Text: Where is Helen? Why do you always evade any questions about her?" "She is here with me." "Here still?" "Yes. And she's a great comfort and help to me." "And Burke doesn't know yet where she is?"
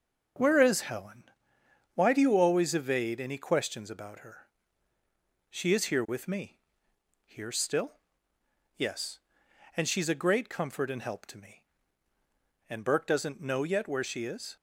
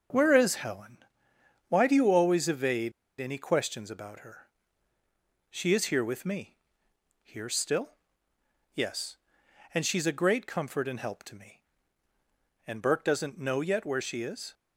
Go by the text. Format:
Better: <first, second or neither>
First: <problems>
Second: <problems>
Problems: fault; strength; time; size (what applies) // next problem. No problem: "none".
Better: first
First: starts louder than the rest; until 2.0 s; 6.5 dB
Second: starts louder than the rest; until 1.8 s; 6.5 dB // pauses between "evade" and "any"; slight; at 2.9 s; 0.27 s long